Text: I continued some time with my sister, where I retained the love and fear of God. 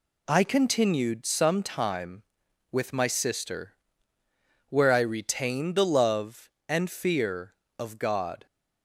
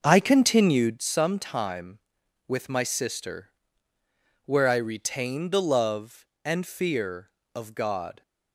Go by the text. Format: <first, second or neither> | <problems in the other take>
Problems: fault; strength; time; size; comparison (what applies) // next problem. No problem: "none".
first | starts louder than the rest; noticeable; until 1.0 s; 6 dB